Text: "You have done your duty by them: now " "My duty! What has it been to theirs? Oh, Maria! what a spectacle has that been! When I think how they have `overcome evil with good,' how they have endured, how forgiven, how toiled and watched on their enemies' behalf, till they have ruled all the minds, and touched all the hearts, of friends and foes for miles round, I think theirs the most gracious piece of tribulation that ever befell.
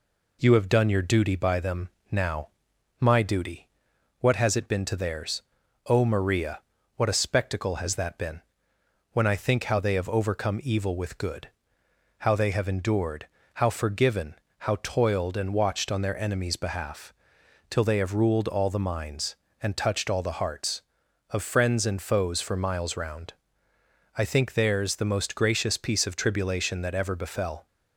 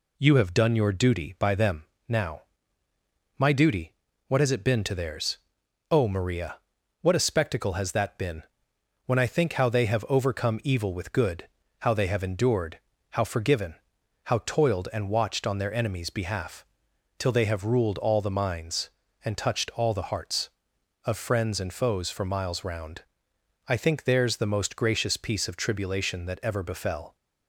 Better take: neither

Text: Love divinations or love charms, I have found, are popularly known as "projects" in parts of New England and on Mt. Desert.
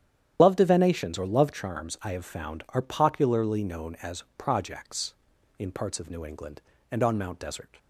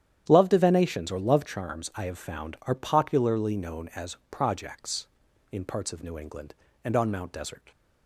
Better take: second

